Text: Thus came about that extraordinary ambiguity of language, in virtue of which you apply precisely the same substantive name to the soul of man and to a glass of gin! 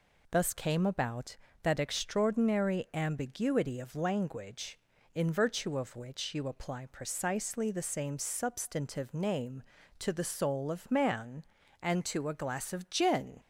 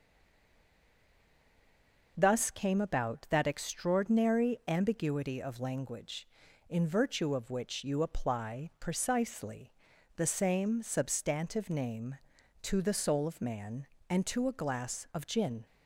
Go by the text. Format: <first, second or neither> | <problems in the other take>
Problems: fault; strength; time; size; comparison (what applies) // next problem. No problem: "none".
first | stays silent before the first word; until 2.1 s; 2.1 s long // pauses between "precisely" and "the"; at 9.7 s; 0.44 s long